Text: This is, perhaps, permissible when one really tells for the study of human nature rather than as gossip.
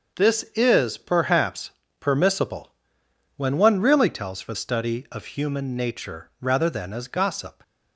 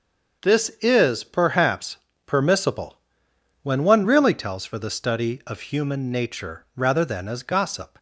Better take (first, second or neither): second